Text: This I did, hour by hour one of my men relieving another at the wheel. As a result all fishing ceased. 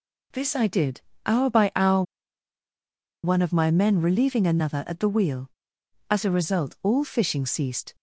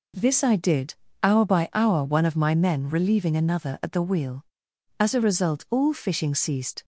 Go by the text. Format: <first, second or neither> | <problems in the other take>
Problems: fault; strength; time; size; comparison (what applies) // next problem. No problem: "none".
second | pauses between "hour" and "one"; at 2.0 s; 1.2 s long